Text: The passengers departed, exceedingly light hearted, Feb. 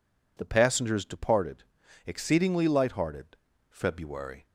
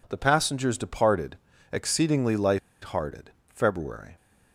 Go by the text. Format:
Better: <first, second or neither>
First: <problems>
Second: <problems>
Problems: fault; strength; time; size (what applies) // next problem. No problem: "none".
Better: first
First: none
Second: pauses between "light" and "hearted"; slight; at 2.5 s; 0.24 s long